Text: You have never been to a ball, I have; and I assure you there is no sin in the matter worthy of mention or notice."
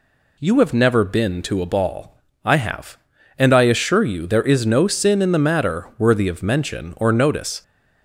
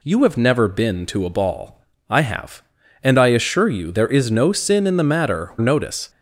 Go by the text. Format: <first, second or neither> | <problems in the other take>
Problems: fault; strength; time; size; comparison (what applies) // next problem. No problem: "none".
first | skips "worthy of mention or"; at 5.5 s